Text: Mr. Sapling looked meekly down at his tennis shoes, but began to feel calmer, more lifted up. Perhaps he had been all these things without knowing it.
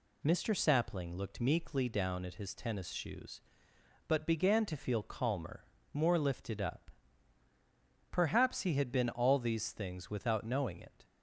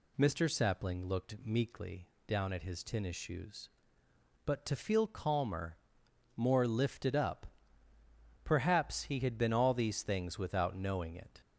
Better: first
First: none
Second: pauses between "meekly" and "down"; slight; at 2.0 s; 0.22 s long // skips "began"; at 4.6 s

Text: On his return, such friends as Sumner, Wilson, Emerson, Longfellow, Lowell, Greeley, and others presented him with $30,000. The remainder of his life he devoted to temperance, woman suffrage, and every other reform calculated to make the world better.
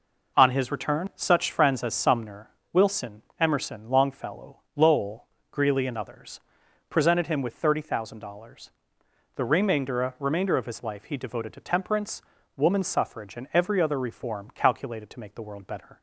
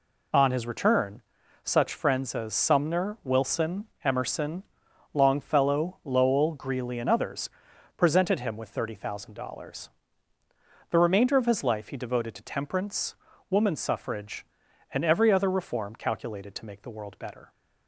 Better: second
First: pauses between "others" and "presented"; noticeable; at 6.3 s; 0.50 s long // says "remainder" twice; at 10.1 s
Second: pauses between "others" and "presented"; noticeable; at 7.4 s; 0.46 s long

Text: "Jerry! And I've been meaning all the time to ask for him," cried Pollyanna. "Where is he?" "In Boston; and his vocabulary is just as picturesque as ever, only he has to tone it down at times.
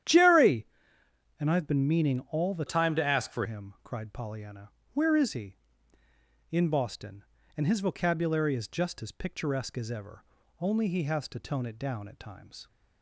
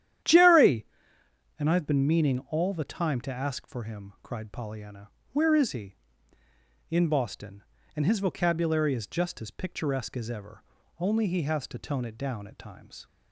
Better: second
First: starts louder than the rest; strong; until 1.7 s; 10.5 dB // changes voice from "time" to "for"; from 2.6 to 3.4 s; 0.8 s long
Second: starts louder than the rest; strong; until 1.9 s; 11 dB

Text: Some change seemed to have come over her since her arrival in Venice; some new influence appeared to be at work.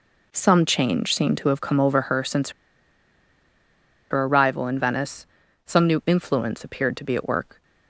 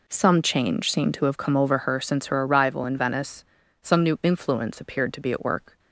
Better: second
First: pauses between "since" and "her"; strong; at 2.5 s; 1.6 s long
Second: none

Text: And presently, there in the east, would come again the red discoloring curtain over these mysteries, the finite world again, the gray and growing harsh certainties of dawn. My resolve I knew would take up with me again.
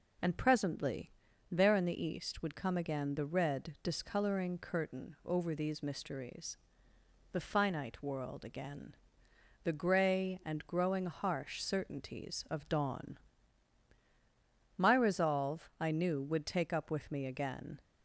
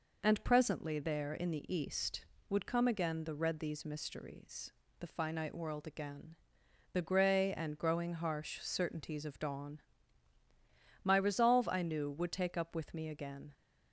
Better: first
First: none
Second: skips "discoloring curtain over"; at 3.5 s

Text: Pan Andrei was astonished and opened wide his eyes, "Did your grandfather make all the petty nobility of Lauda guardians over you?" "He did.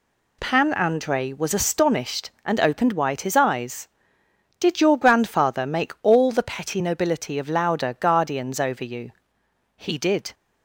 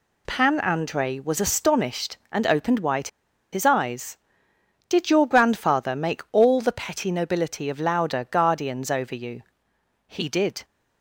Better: first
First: none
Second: pauses between "wide" and "his"; at 3.0 s; 0.44 s long

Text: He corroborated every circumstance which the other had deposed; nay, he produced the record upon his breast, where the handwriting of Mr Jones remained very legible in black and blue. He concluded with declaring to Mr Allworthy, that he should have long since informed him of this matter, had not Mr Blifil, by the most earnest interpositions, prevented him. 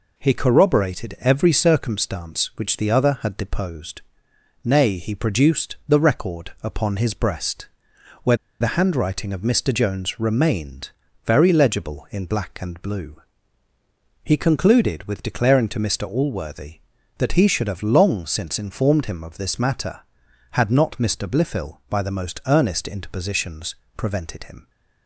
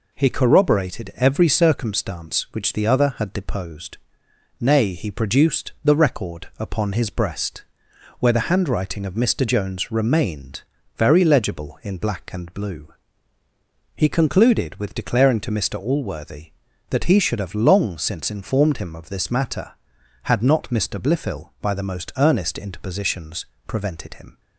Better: second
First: pauses between "where" and "the"; slight; at 8.3 s; 0.24 s long // pauses between "remained" and "very"; slight; at 10.9 s; 0.34 s long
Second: pauses between "remained" and "very"; slight; at 10.6 s; 0.34 s long

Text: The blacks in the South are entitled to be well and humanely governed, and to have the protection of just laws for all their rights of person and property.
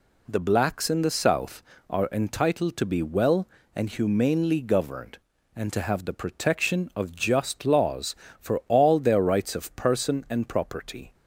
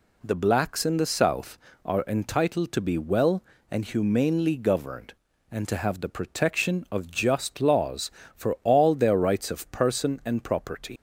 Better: first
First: none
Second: leaves "property" unfinished; at 10.9 s; 125 ms

